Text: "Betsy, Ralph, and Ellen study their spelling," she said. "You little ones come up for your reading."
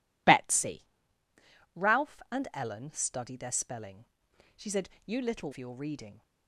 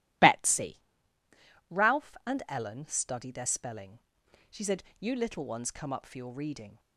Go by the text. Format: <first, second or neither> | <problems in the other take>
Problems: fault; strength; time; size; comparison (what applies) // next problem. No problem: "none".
second | skips "ones come up"; at 5.5 s